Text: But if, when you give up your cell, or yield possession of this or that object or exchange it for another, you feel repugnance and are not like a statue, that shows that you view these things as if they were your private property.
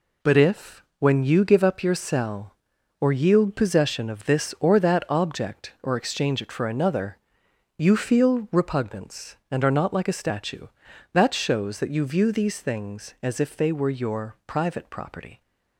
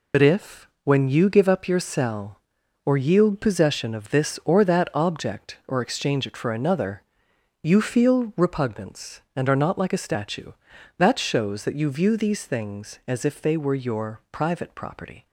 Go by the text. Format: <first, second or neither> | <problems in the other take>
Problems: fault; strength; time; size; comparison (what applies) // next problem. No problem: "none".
first | loses the start of "But"; at 0.1 s; 65 ms